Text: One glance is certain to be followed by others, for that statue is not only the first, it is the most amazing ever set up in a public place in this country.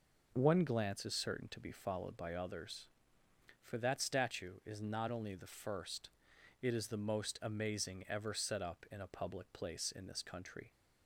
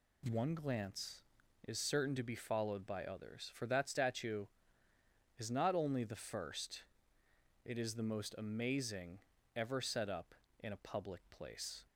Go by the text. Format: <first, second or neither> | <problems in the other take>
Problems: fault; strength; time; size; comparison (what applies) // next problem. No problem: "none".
first | pauses between "amazing" and "ever"; at 9.1 s; 0.38 s long // stops before "in this country"; at 11.8 s